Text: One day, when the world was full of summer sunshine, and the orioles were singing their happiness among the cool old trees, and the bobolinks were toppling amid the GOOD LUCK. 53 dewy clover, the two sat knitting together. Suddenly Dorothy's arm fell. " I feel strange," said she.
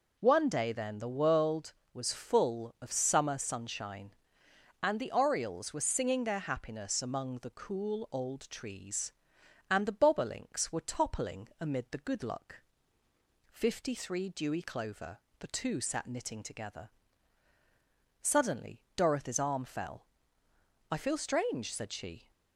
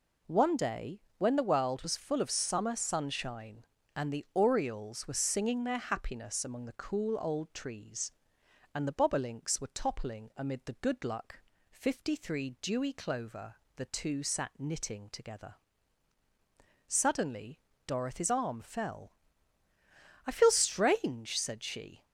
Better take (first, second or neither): second